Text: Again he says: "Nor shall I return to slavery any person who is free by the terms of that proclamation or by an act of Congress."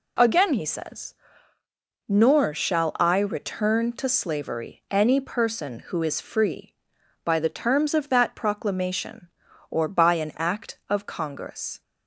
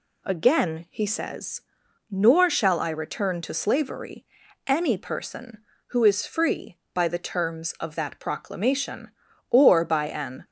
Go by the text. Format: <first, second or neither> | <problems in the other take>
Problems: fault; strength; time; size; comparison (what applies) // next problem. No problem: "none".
first | pauses between "slavery" and "any"; at 4.2 s; 0.44 s long // stops before "act of Congress"; at 10.4 s